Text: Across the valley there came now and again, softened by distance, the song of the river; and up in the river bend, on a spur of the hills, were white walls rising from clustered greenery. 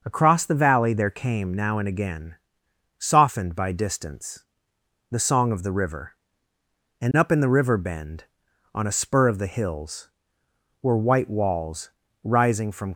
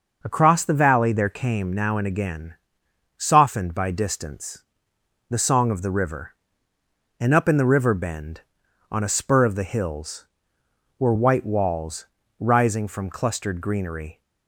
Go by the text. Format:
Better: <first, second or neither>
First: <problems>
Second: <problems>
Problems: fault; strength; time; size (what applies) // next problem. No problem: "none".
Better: second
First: pauses between "walls" and "rising"; slight; at 11.8 s; 0.34 s long // stops before "clustered greenery"; at 12.9 s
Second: pauses between "walls" and "rising"; slight; at 12.0 s; 0.34 s long